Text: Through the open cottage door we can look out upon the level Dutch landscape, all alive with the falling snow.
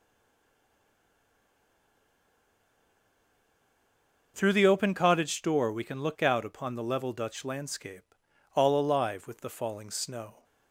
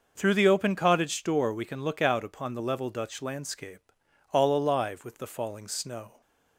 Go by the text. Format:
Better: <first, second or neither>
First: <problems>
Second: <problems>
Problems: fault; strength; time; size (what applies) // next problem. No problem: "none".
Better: second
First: stays silent before the first word; strong; until 4.3 s; 4.3 s long // starts louder than the rest; noticeable; until 5.3 s; 6 dB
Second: starts louder than the rest; noticeable; until 1.1 s; 6 dB